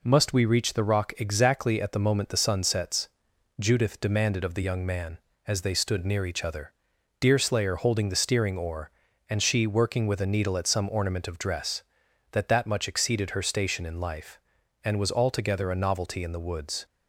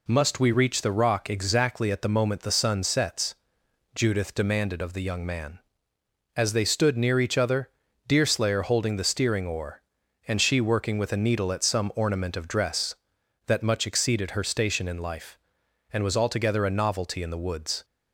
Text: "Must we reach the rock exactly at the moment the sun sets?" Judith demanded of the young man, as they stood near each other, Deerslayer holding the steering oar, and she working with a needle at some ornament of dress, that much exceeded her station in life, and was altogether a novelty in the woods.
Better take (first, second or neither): second